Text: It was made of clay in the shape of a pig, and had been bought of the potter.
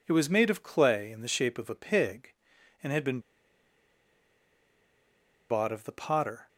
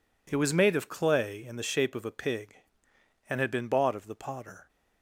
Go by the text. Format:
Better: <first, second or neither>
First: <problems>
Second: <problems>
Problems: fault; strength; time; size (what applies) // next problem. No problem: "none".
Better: second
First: pauses between "been" and "bought"; strong; at 3.1 s; 2.3 s long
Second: none